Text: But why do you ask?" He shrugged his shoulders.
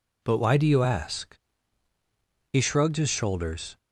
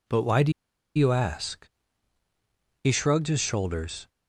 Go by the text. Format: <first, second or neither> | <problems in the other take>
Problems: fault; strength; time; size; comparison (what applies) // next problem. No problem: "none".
first | pauses between "do" and "you"; at 0.5 s; 0.43 s long